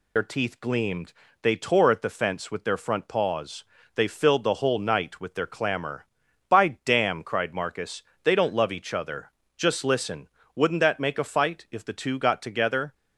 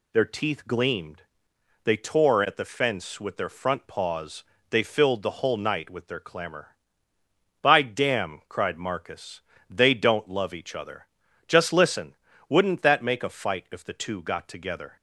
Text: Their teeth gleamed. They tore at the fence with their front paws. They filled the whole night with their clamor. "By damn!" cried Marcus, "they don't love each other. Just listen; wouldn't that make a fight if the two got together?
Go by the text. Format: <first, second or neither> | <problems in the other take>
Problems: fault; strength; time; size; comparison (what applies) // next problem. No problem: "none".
second | loses the start of "Their"; at 0.1 s; 65 ms